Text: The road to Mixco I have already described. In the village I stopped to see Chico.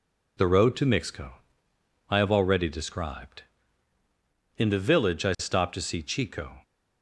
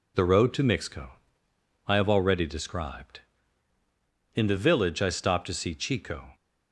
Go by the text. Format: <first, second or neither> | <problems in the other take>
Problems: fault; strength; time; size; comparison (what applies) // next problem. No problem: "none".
neither | pauses between "Mixco" and "I"; noticeable; the same in both